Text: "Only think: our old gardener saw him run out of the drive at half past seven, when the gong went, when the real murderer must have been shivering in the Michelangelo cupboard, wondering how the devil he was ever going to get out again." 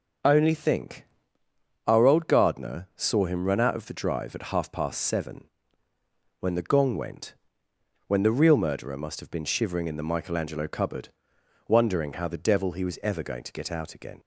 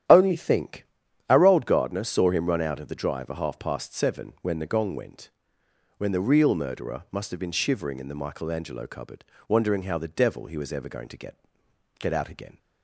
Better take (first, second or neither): first